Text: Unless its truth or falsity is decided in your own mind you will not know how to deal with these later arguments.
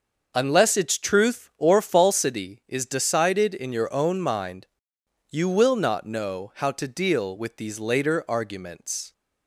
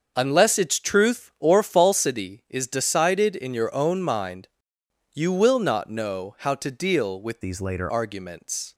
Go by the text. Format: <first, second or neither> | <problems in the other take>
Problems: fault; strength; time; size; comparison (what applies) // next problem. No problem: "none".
first | starts louder than the rest; until 1.1 s; 6.5 dB; also in the first // pauses between "mind" and "you"; noticeable; at 4.4 s; 0.66 s long; noticeable in the first // changes voice from "these" to "later"; from 7.4 to 7.9 s; 0.5 s long